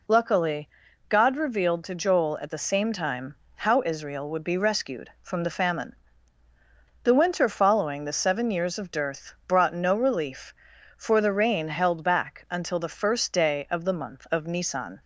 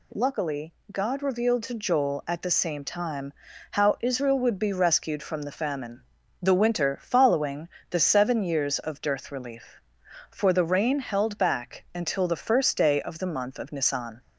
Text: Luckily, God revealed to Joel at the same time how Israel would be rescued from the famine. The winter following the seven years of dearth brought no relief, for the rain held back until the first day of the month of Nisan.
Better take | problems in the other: first | pauses between "time" and "how"; at 3.3 s; 0.40 s long; slight in the first // pauses between "following" and "the"; slight; at 7.6 s; 0.22 s long // skips "brought no"; at 9.3 s

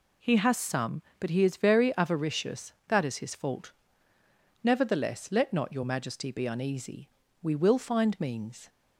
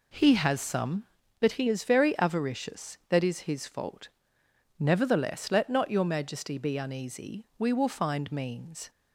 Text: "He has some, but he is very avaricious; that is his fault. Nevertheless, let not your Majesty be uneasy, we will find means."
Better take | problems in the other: neither | none

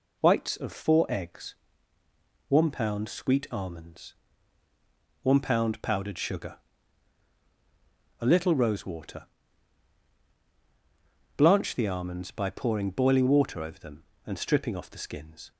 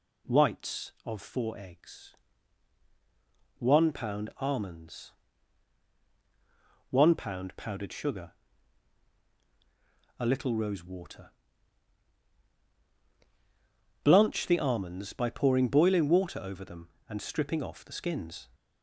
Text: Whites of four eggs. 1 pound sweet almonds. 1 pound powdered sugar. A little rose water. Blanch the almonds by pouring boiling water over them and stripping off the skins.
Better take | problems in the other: first | skips "sweet"; at 4.3 s

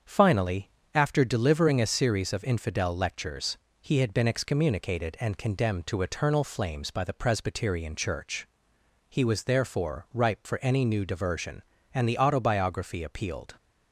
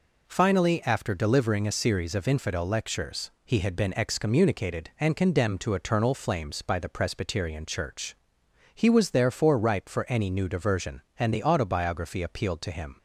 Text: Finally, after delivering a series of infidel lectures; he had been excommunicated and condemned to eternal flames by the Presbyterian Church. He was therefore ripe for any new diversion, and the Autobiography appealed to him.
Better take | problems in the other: second | starts louder than the rest; strong; until 1.2 s; 7 dB // stops before "to him"; at 13.5 s

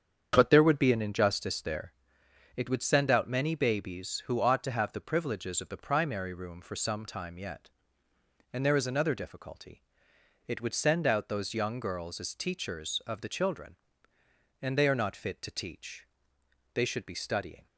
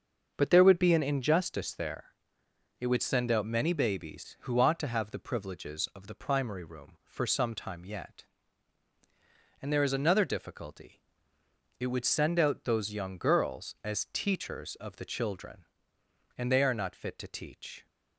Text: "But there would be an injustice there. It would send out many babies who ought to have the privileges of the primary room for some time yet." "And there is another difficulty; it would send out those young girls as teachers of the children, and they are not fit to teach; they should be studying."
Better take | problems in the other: first | starts louder than the rest; until 1.3 s; 6.5 dB; strong in the first // stops before "they should be studying"; at 17.8 s

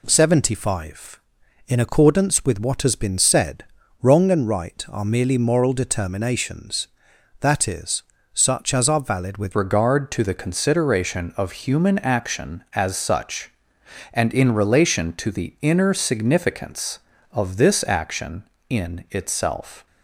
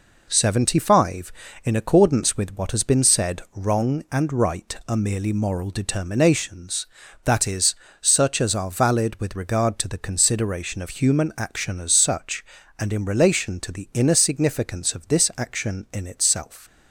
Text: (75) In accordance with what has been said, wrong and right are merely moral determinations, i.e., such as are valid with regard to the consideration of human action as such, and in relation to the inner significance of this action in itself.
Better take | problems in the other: second | changes voice at "regard"; from 9.5 s on; 10.3 s long

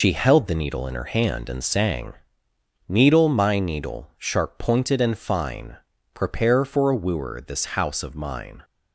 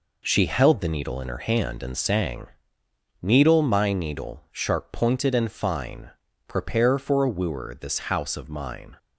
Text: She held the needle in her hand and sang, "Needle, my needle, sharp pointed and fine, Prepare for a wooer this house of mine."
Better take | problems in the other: second | loses the start of "She"; at 0.0 s; 100 ms

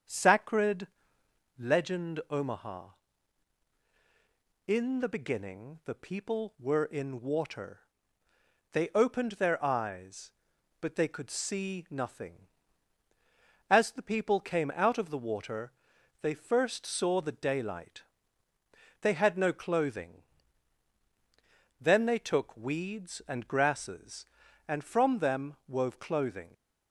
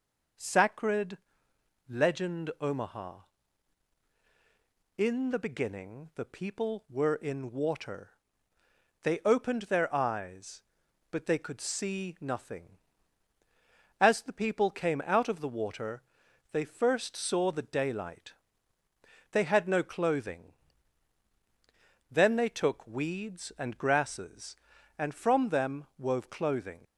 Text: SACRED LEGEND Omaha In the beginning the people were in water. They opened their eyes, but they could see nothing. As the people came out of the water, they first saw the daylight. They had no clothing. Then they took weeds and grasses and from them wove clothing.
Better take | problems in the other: second | starts louder than the rest; strong; until 1.6 s; 7.5 dB // pauses between "SACRED" and "LEGEND"; noticeable; at 0.8 s; 0.72 s long; noticeable in the second

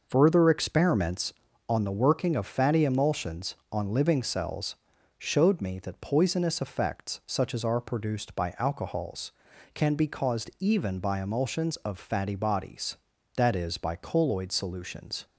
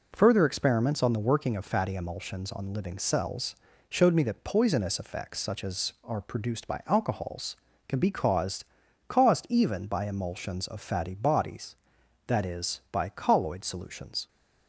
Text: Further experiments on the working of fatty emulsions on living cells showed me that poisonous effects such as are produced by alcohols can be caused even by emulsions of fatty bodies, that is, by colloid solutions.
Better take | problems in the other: first | pauses between "cells" and "showed"; slight; at 3.5 s; 0.34 s long; also in the first // says "caused" twice; at 9.0 s

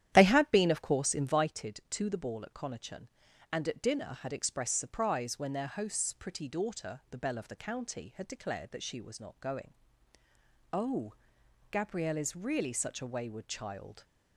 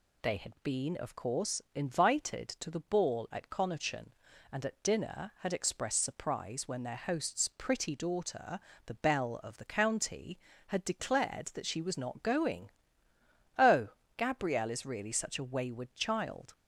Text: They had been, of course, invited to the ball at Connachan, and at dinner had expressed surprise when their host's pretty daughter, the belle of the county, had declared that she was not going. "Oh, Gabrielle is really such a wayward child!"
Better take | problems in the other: second | starts louder than the rest; strong; until 1.5 s; 11.5 dB

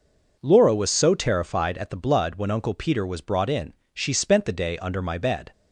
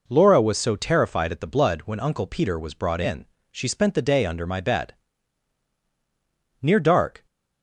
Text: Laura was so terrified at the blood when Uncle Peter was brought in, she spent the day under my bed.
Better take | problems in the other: first | goes on to say "Near dark"; noticeable; from 6.6 s on; 0.64 s long

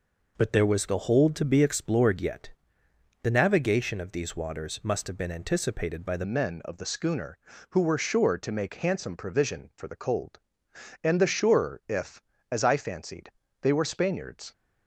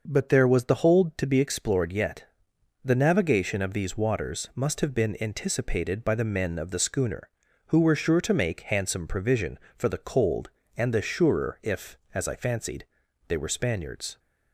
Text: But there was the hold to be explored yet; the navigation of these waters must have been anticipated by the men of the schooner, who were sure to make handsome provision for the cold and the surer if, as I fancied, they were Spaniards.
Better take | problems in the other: second | changes voice at "men"; from 6.2 s on; 8.3 s long

